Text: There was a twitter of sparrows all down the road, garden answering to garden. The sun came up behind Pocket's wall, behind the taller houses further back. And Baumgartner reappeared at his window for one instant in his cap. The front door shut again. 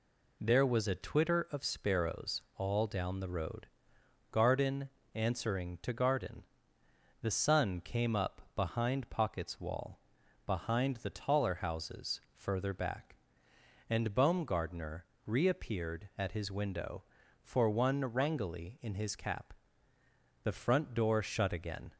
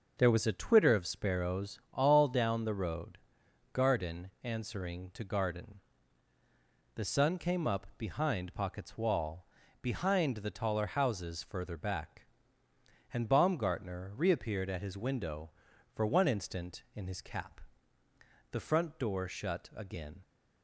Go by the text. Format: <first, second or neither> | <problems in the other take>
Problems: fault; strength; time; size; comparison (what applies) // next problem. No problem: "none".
second | pauses between "sparrows" and "all"; slight; at 2.4 s; 0.16 s long // pauses between "garden" and "answering"; slight; at 4.8 s; 0.24 s long // pauses between "Baumgartner" and "reappeared"; slight; at 15.0 s; 0.20 s long // says "wrangly" for "instant"; at 18.0 s